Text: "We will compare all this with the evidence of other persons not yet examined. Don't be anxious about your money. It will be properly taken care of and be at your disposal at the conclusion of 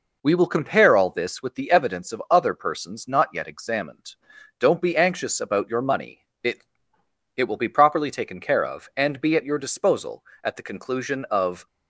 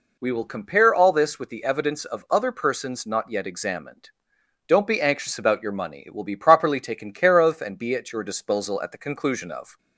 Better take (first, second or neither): second